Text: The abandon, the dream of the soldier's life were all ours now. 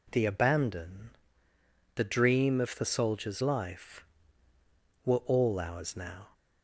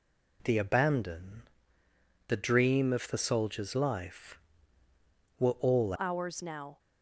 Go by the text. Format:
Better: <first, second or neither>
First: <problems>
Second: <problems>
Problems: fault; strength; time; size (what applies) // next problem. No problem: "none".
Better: first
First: none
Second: changes voice at "ours"; from 5.9 s on; 0.8 s long